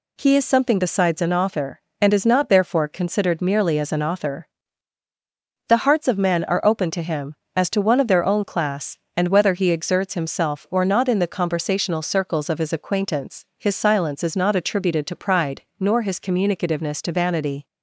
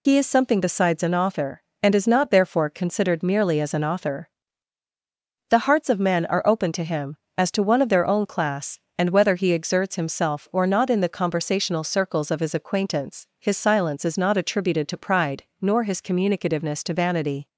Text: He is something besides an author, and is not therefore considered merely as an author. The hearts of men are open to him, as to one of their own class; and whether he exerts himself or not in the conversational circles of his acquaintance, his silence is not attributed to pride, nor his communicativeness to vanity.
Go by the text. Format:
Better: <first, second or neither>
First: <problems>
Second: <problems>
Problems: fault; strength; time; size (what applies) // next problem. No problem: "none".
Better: first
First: none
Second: loses the start of "He"; at 0.0 s; 55 ms